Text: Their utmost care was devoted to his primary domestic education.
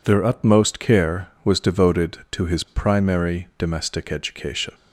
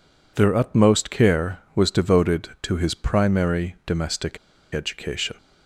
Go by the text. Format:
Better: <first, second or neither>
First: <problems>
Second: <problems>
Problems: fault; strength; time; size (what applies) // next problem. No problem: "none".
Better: first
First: none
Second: pauses between "domestic" and "education"; at 4.3 s; 0.37 s long